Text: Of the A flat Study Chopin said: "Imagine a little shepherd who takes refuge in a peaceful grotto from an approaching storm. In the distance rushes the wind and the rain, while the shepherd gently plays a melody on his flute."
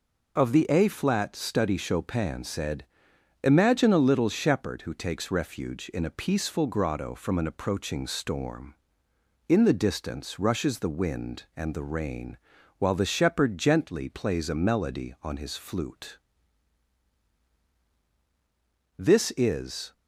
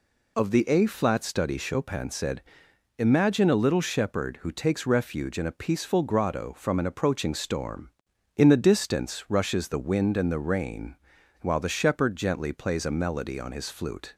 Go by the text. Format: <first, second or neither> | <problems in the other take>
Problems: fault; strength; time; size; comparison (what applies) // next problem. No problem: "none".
second | goes on to say "This is"; noticeable; from 18.9 s on; 0.94 s long